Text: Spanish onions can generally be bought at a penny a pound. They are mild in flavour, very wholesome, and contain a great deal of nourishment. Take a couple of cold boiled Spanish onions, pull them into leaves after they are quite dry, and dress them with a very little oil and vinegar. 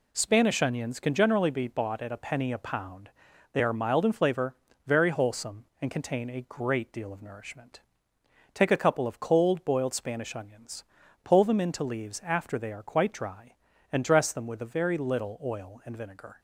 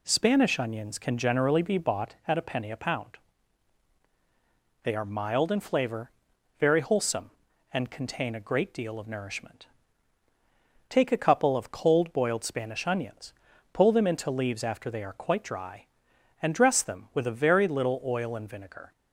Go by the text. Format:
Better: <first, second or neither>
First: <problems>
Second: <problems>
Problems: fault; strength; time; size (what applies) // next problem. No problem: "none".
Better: neither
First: none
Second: none